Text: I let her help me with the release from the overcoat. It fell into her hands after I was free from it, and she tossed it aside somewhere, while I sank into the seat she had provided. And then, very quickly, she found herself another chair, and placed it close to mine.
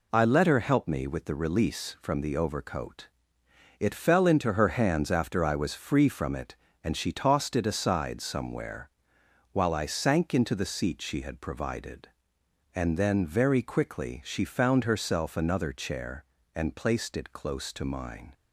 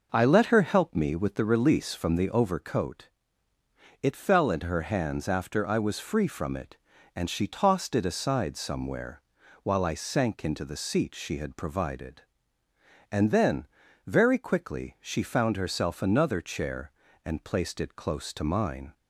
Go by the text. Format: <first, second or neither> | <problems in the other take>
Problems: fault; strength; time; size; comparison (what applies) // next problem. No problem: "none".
neither | none